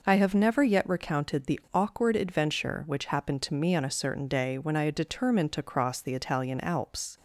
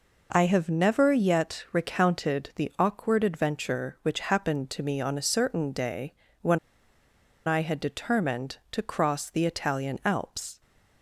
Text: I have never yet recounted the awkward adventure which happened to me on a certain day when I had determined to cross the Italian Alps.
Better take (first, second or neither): first